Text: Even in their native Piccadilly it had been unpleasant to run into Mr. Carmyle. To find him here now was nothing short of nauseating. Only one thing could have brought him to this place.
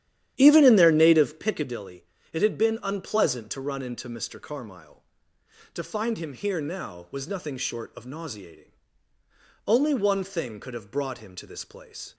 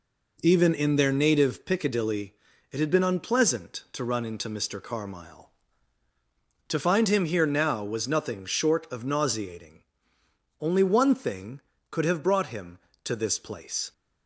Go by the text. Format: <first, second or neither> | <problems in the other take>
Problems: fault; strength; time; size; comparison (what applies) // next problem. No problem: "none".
second | starts louder than the rest; strong; until 1.6 s; 11 dB // pauses between "Piccadilly" and "it"; slight; at 2.0 s; 0.26 s long; slight in the second